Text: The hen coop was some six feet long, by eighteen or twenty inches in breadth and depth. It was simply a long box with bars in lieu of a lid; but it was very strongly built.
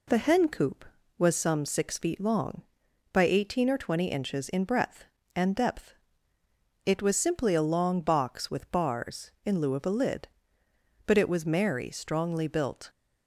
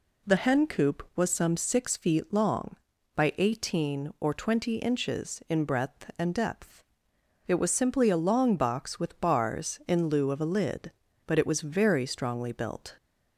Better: second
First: says "merry" for "very"; at 11.4 s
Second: none

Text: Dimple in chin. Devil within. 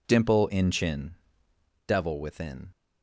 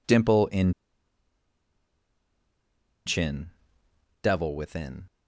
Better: first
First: none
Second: pauses between "in" and "chin"; strong; at 0.7 s; 2.3 s long

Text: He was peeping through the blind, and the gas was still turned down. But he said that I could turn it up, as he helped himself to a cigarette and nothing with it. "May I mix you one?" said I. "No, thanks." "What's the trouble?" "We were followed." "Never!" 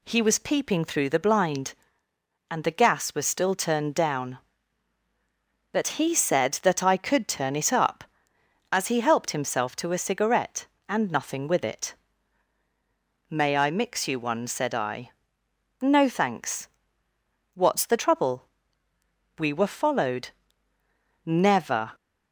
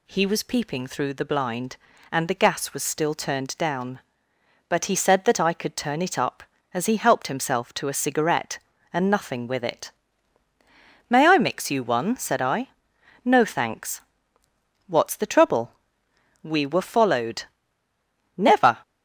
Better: neither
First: none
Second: none

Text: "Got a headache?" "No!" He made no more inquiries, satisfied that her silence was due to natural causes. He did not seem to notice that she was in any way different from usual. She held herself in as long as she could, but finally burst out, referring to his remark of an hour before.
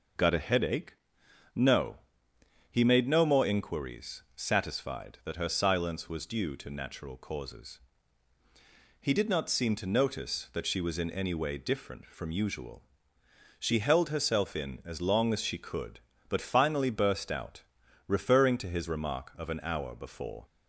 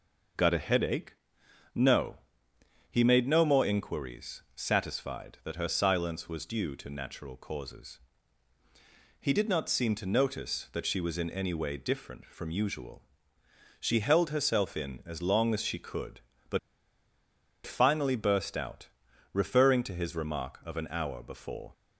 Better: first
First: none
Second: pauses between "but" and "finally"; at 16.5 s; 1.0 s long

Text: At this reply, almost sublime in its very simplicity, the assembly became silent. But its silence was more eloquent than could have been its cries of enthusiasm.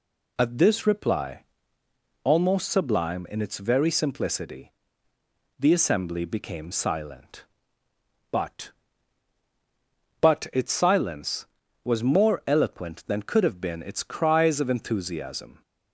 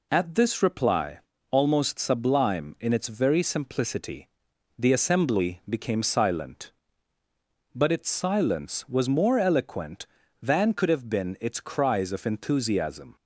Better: second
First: says "But" twice; at 10.2 s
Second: none

